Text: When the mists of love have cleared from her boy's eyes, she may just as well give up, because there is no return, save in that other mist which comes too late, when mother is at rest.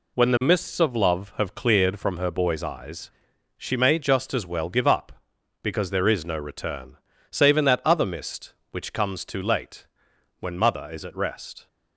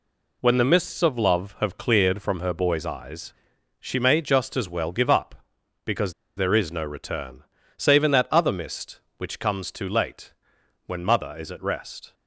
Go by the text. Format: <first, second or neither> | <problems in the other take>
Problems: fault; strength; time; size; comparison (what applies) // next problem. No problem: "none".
first | pauses between "because" and "there"; slight; at 6.1 s; 0.24 s long